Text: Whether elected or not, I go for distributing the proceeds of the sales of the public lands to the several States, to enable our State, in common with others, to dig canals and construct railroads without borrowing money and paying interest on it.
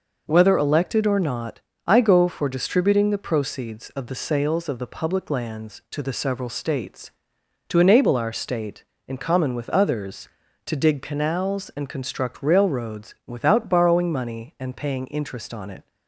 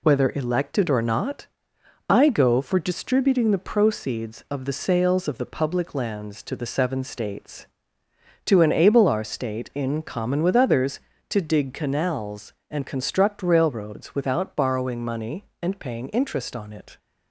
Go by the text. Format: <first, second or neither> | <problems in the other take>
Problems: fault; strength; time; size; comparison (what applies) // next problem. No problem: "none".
first | says "seven" for "several"; at 6.6 s